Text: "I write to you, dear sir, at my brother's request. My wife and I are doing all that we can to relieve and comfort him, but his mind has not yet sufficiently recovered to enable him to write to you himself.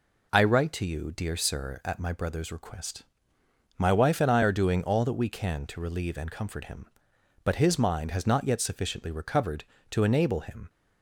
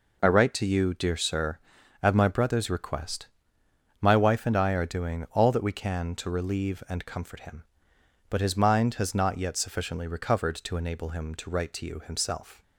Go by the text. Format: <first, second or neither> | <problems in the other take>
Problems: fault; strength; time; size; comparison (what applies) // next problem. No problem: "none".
second | stops before "to write to you himself"; at 10.6 s